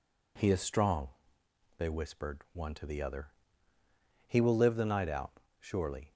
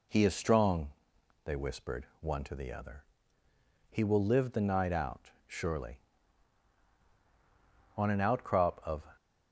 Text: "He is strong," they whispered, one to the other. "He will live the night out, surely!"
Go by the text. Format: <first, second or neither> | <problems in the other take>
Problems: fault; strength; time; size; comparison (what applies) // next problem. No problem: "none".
first | goes on to say "On an outcrop of"; noticeable; from 7.9 s on; 1.1 s long